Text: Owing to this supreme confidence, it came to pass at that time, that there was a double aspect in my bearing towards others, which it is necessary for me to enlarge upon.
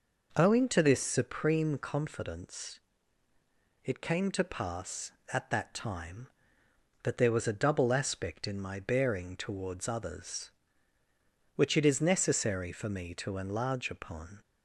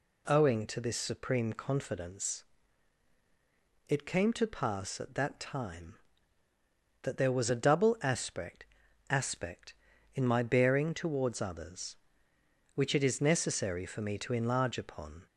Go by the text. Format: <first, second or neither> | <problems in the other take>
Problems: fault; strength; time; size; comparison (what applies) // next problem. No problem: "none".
first | says "aspect" twice; at 9.0 s